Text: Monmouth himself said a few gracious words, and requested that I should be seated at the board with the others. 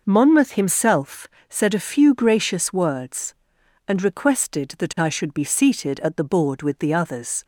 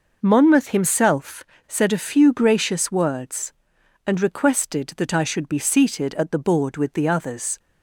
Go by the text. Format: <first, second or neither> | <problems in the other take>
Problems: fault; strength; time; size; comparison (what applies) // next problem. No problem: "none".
neither | pauses between "himself" and "said"; slight; the same in both